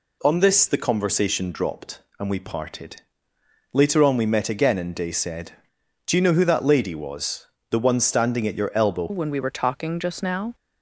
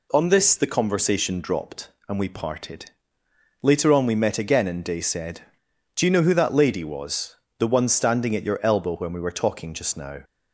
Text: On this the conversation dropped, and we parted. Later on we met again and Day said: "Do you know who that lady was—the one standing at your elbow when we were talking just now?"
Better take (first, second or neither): second